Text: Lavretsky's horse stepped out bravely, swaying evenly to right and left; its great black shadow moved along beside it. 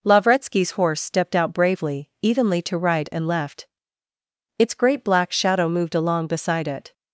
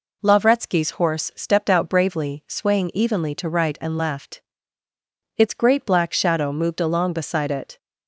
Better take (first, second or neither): second